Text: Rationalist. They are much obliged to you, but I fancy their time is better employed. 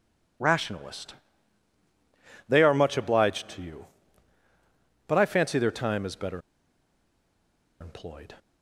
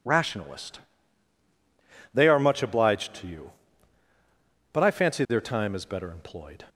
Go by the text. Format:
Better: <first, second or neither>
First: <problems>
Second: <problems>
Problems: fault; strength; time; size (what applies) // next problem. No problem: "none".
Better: second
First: pauses between "better" and "employed"; strong; at 6.4 s; 1.4 s long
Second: none